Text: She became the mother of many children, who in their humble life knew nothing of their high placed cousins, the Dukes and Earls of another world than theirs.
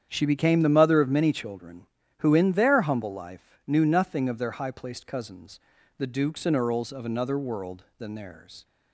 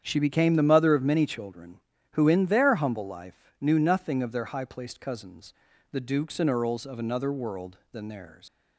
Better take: first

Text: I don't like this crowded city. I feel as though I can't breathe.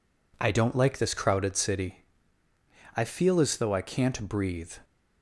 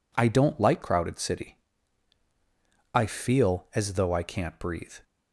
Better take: first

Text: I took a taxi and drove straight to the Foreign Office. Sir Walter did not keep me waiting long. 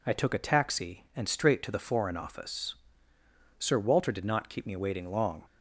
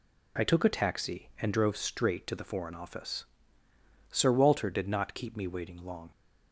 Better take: second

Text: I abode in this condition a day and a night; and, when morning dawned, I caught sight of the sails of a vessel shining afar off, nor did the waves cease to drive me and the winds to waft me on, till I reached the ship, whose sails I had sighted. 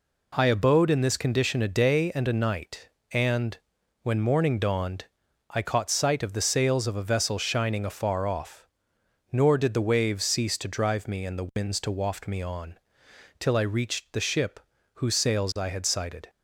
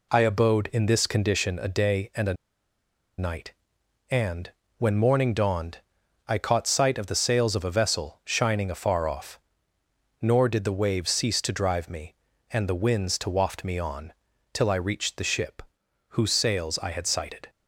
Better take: first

